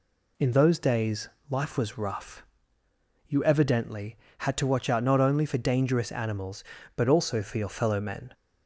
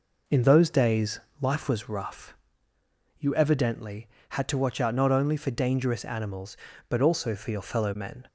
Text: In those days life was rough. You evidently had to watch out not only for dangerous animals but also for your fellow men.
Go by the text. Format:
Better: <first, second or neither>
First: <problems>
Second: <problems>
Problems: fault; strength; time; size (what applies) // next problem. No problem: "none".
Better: first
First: pauses between "days" and "life"; slight; at 1.2 s; 0.20 s long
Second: starts louder than the rest; noticeable; until 1.9 s; 5 dB // pauses between "days" and "life"; slight; at 1.2 s; 0.20 s long